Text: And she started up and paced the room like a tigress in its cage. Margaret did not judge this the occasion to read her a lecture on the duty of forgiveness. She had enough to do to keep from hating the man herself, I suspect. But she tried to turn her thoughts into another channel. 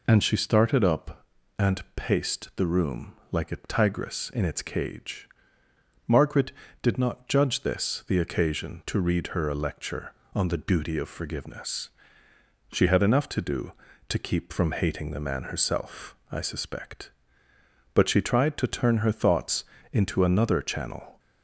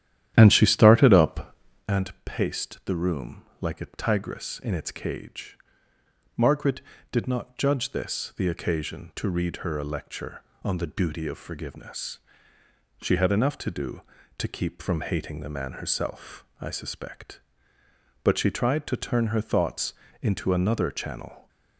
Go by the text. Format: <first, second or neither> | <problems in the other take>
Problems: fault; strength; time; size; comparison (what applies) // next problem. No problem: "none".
first | starts louder than the rest; strong; until 1.9 s; 11 dB // pauses between "room" and "like"; slight; at 3.4 s; 0.16 s long; slight in the first // pauses between "thoughts" and "into"; slight; at 19.9 s; 0.28 s long; slight in the first